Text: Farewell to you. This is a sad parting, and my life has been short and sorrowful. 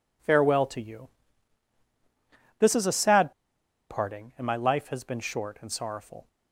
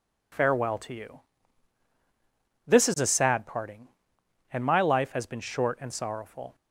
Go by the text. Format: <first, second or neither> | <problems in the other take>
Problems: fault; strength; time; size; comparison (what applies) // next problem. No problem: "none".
second | pauses between "sad" and "parting"; noticeable; at 3.3 s; 0.57 s long